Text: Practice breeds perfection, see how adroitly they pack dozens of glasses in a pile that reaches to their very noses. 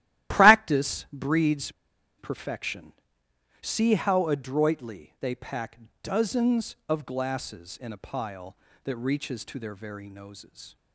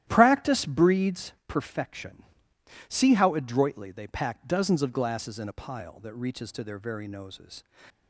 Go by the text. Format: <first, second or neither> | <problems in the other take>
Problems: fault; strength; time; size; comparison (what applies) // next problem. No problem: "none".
second | starts louder than the rest; strong; until 1.4 s; 13.5 dB; strong in the second // pauses between "breeds" and "perfection"; noticeable; at 1.7 s; 0.47 s long // pauses between "pack" and "dozens"; slight; at 5.7 s; 0.24 s long